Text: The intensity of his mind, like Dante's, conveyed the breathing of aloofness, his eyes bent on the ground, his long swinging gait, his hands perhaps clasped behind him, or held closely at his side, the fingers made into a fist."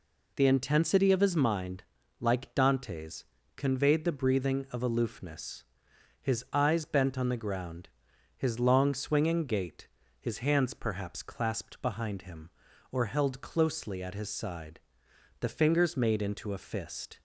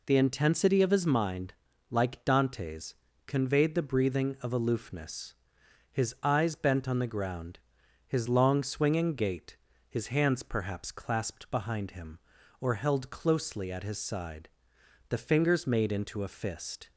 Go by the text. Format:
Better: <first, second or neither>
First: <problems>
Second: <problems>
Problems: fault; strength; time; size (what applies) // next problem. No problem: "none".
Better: neither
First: none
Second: none